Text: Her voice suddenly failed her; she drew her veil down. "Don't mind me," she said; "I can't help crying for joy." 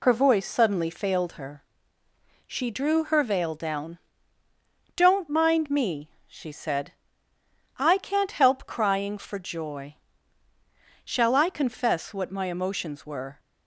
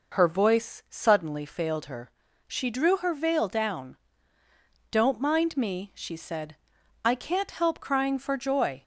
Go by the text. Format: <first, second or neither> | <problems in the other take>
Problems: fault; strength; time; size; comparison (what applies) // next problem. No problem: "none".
second | goes on to say "Shall I confess what my emotions were"; strong; from 11.0 s on; 2.3 s long